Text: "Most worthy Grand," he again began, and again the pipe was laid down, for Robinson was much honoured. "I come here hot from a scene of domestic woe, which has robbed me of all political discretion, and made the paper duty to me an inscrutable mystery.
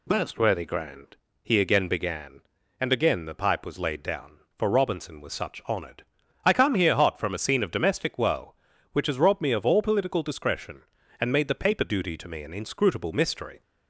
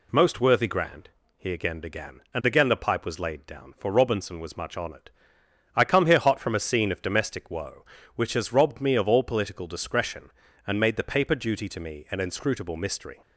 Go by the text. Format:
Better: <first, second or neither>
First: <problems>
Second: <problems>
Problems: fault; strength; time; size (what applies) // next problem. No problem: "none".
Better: second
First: says "such" for "much"; at 5.3 s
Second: none